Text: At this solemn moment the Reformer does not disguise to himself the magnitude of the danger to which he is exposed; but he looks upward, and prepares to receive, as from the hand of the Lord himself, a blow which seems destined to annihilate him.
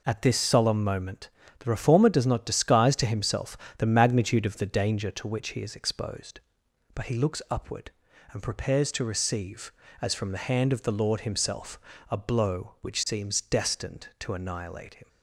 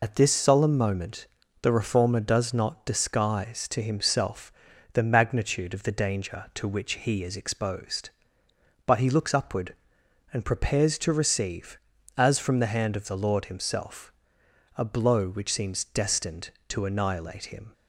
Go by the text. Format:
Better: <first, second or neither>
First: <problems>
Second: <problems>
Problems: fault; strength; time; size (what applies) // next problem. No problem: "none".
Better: first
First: pauses between "moment" and "the"; slight; at 1.2 s; 0.30 s long // pauses between "himself" and "the"; slight; at 3.5 s; 0.20 s long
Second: loses the start of "At"; at 0.0 s; 75 ms // pauses between "moment" and "the"; slight; at 1.2 s; 0.36 s long // pauses between "himself" and "the"; at 4.5 s; 0.40 s long